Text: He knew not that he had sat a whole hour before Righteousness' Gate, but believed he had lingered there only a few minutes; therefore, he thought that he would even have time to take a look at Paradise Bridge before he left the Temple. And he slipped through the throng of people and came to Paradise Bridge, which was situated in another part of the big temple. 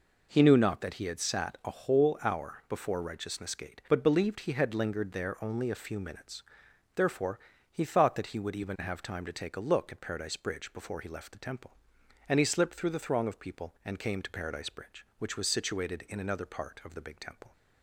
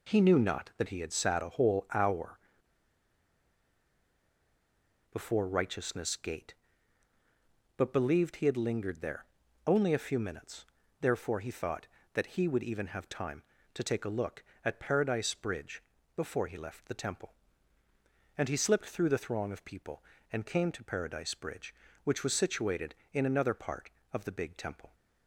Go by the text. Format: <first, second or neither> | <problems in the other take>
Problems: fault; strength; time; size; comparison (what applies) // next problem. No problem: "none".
first | pauses between "hour" and "before"; strong; at 2.3 s; 2.7 s long // pauses between "there" and "only"; at 9.2 s; 0.40 s long // pauses between "Bridge" and "before"; slight; at 15.8 s; 0.34 s long